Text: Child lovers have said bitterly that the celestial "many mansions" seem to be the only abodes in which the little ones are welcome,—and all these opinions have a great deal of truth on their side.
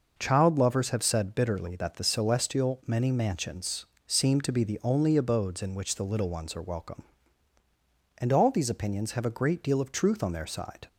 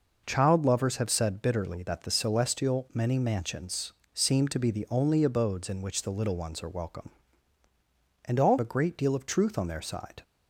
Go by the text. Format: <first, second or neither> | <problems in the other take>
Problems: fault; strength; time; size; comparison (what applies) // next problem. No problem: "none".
first | pauses between "mansions" and "seem"; slight; at 3.9 s; 0.22 s long; slight in the first // skips "these opinions have"; at 8.5 s